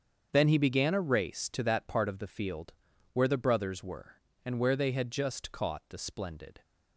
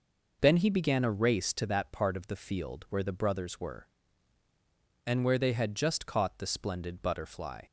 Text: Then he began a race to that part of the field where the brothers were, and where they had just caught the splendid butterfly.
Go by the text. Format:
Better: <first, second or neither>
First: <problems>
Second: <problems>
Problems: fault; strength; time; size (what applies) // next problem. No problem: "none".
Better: second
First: starts louder than the rest; strong; until 1.3 s; 7 dB // pauses between "field" and "where"; at 2.7 s; 0.40 s long // stops before "butterfly"; at 6.6 s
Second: none